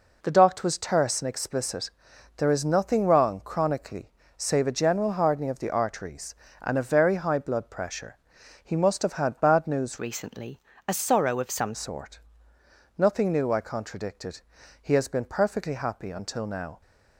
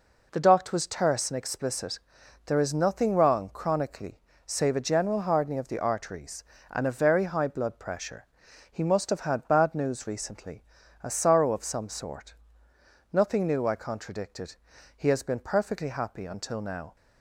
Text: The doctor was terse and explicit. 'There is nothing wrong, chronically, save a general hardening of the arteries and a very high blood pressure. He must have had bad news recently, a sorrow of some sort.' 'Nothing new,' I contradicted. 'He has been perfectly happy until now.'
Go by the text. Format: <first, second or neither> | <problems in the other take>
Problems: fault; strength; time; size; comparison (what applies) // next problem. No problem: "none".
second | changes voice from "recently" to "some"; from 9.9 to 11.7 s; 1.8 s long